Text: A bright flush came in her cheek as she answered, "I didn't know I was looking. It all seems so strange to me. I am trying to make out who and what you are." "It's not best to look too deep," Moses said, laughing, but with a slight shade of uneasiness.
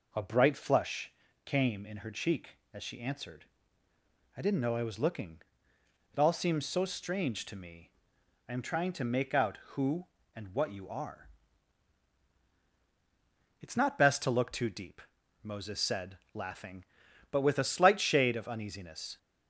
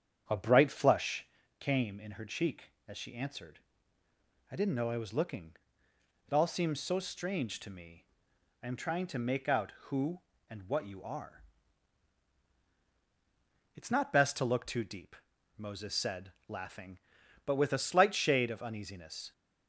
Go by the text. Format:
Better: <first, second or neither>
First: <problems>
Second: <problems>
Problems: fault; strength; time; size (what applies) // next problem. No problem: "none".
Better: first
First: pauses between "flush" and "came"; slight; at 1.0 s; 0.36 s long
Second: starts louder than the rest; strong; until 1.4 s; 8.5 dB // pauses between "flush" and "came"; slight; at 1.2 s; 0.36 s long